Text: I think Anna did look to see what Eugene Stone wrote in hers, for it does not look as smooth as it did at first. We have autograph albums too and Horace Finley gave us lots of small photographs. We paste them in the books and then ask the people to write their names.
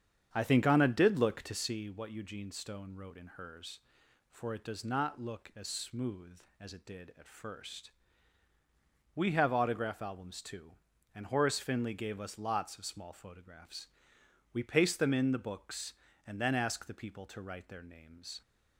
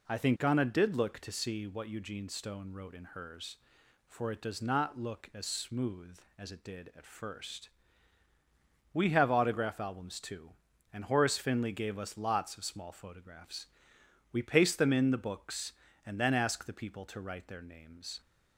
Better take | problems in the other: second | starts louder than the rest; strong; until 1.8 s; 8 dB

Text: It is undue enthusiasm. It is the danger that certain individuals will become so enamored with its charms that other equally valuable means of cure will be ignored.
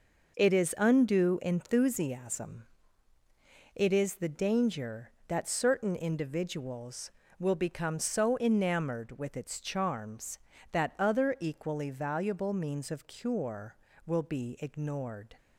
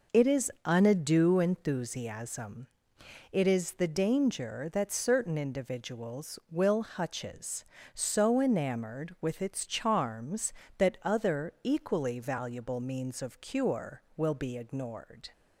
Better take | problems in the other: first | says "hutches" for "become"; at 6.8 s

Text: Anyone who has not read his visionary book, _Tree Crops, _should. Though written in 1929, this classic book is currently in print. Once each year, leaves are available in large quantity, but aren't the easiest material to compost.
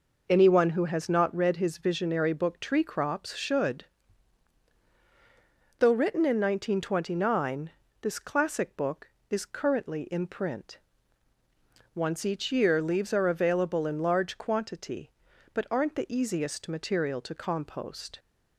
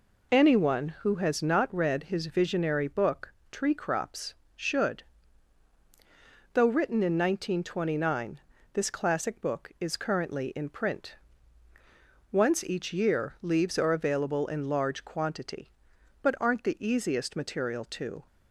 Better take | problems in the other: first | stops before "compost"; at 18.2 s

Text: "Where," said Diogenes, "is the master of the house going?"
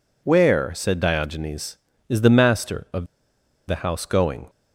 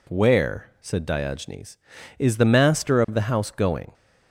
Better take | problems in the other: second | pauses between "of" and "the"; noticeable; at 3.0 s; 0.63 s long

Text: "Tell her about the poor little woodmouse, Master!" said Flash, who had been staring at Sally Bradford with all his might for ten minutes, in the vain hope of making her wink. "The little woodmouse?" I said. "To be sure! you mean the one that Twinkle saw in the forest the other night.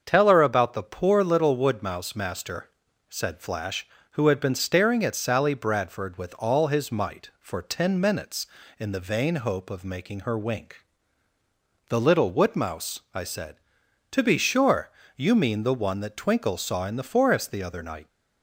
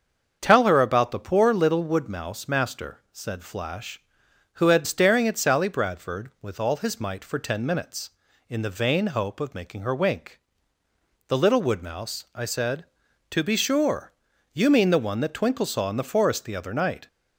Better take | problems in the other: first | starts louder than the rest; until 1.4 s; 7 dB; also in the first // skips "been"; at 4.8 s

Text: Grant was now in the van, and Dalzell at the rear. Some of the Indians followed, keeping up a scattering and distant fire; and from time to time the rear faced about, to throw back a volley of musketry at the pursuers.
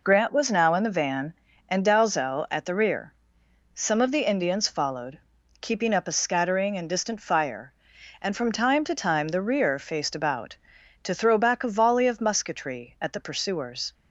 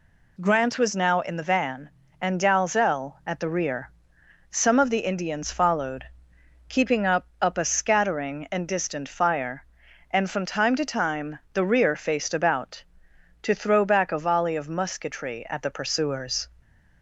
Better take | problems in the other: first | says "up" twice; at 7.3 s // pauses between "time" and "the"; slight; at 11.3 s; 0.16 s long

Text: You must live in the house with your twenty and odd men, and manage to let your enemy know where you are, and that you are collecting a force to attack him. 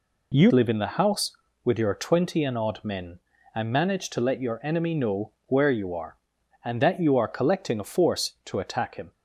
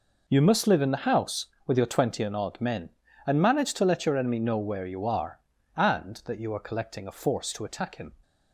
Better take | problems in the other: second | skips "must"; at 0.5 s // pauses between "know" and "where"; slight; at 5.2 s; 0.16 s long

